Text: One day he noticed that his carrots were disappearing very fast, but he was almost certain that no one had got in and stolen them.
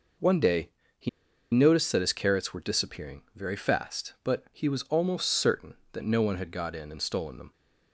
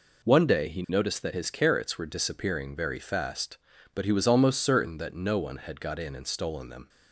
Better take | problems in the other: second | pauses between "day" and "he"; slight; at 0.6 s; 0.28 s long // pauses between "he" and "noticed"; at 1.0 s; 0.44 s long

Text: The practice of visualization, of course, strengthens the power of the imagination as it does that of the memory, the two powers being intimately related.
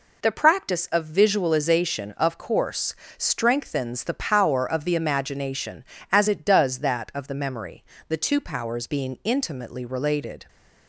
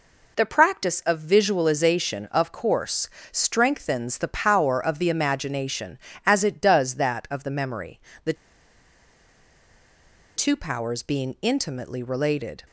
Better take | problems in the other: first | pauses between "the" and "two"; strong; at 8.3 s; 2.0 s long

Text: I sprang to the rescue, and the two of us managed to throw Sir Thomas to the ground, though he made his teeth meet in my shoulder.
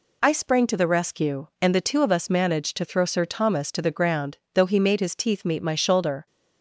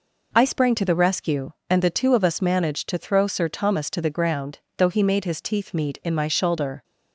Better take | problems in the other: second | skips "in"; at 5.6 s

